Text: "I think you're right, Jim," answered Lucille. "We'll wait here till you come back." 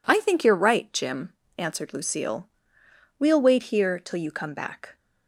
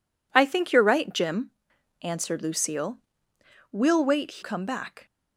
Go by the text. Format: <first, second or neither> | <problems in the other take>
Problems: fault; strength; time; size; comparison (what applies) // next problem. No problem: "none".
first | skips "here till you"; at 4.4 s